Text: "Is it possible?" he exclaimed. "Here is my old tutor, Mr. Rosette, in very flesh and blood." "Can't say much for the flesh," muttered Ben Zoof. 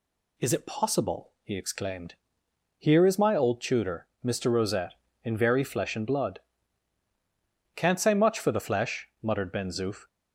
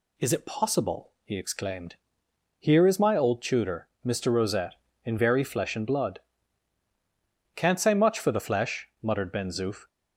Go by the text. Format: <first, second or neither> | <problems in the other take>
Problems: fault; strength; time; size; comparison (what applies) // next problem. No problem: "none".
neither | none